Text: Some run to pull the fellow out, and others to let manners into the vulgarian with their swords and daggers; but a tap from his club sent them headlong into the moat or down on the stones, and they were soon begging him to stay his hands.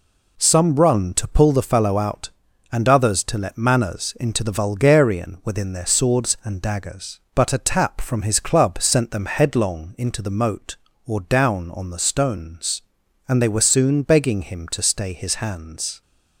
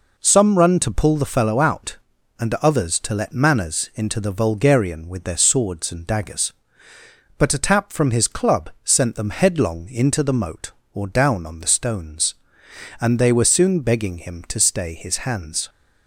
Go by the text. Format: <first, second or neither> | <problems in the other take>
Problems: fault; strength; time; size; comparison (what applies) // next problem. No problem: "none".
second | says "within" for "with"; at 5.4 s